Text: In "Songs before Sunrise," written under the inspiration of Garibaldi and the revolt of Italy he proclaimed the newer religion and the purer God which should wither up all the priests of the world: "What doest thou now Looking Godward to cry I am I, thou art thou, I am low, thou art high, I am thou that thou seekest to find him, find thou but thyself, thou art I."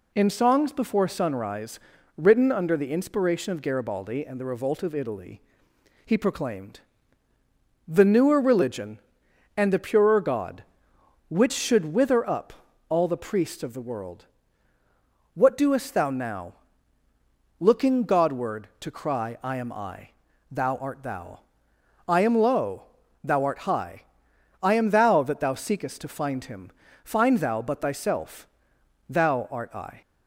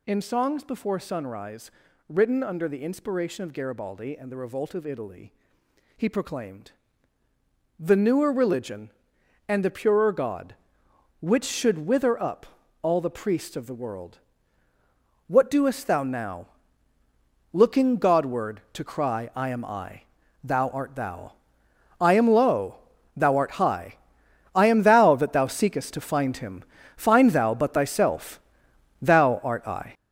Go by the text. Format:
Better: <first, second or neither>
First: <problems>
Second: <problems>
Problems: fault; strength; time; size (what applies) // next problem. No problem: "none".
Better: first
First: pauses between "Italy" and "he"; noticeable; at 5.4 s; 0.64 s long // pauses between "proclaimed" and "the"; at 6.8 s; 1.0 s long // pauses between "up" and "all"; at 12.5 s; 0.38 s long // pauses between "now" and "Looking"; at 16.5 s; 1.0 s long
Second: gets louder; strong; throughout; 8.5 dB // pauses between "Italy" and "he"; noticeable; at 5.3 s; 0.64 s long // pauses between "proclaimed" and "the"; at 6.7 s; 1.0 s long // pauses between "up" and "all"; at 12.4 s; 0.38 s long // pauses between "now" and "Looking"; at 16.4 s; 1.0 s long